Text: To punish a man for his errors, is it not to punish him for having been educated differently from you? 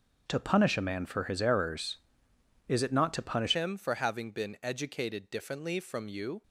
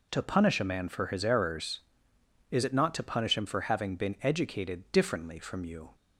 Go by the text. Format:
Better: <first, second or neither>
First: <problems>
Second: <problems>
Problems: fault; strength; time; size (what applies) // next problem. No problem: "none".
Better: second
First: changes voice at "him"; from 3.5 s on; 2.9 s long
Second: none